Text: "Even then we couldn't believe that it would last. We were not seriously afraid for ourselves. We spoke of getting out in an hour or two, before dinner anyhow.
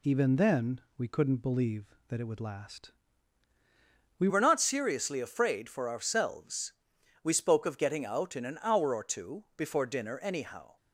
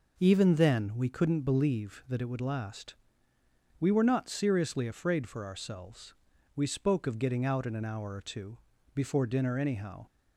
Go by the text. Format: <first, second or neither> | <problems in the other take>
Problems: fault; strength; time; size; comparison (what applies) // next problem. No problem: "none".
second | pauses between "then" and "we"; slight; at 0.8 s; 0.16 s long // changes voice at "were"; from 4.2 s on; 6.5 s long